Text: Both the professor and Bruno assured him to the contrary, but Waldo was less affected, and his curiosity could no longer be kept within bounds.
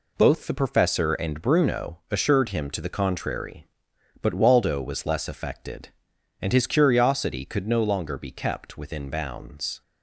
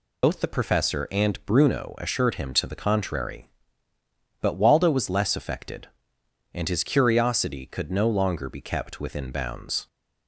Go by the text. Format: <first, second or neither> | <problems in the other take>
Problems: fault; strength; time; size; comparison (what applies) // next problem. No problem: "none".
first | loses the start of "Both"; at 0.2 s; 85 ms